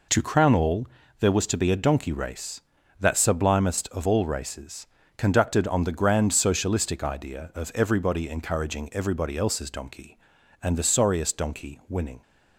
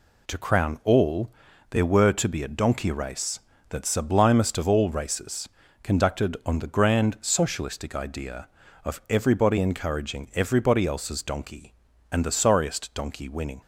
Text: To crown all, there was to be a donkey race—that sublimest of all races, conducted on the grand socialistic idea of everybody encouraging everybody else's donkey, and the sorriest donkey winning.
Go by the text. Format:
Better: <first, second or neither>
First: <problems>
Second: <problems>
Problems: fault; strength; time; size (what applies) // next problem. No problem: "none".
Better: first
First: none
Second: says "were" for "was"; at 1.8 s